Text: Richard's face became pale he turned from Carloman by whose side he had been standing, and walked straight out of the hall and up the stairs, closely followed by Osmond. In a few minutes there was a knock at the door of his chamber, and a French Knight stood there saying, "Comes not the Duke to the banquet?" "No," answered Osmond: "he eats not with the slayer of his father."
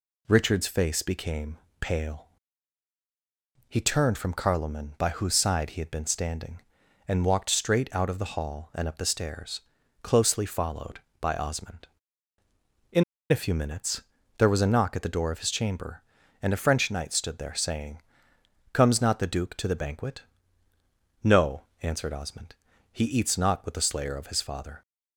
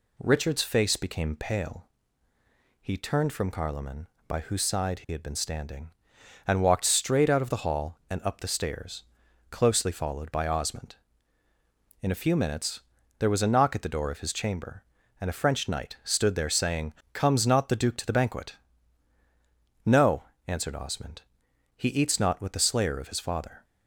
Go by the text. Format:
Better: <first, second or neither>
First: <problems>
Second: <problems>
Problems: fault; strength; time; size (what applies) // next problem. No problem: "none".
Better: second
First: pauses between "became" and "pale"; slight; at 1.5 s; 0.24 s long // pauses between "pale" and "he"; strong; at 2.2 s; 1.4 s long // pauses between "In" and "a"; slight; at 13.0 s; 0.27 s long // pauses between "minutes" and "there"; slight; at 14.0 s; 0.36 s long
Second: pauses between "pale" and "he"; noticeable; at 1.8 s; 0.94 s long // pauses between "minutes" and "there"; at 12.7 s; 0.38 s long